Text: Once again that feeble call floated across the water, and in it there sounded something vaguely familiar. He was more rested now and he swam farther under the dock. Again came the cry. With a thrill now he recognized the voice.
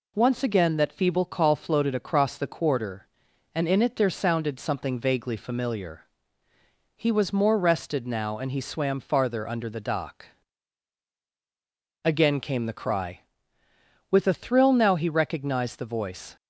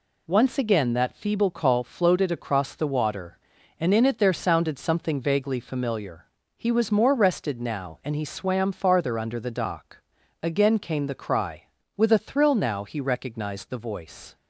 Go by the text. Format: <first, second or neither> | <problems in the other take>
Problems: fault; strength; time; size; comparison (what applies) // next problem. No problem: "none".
second | says "quarter" for "water"; at 2.4 s